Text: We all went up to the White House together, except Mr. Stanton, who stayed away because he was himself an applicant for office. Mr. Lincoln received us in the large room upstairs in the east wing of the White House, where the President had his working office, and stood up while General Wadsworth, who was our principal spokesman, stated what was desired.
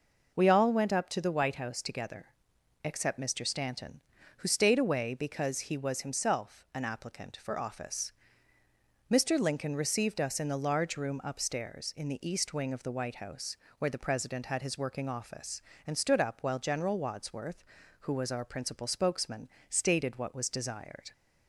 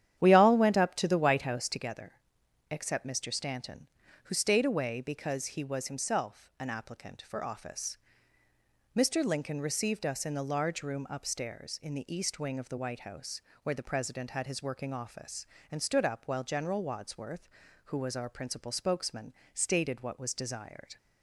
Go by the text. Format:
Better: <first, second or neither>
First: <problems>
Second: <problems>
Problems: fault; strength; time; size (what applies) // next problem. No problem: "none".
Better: first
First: none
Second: starts louder than the rest; strong; until 1.9 s; 10 dB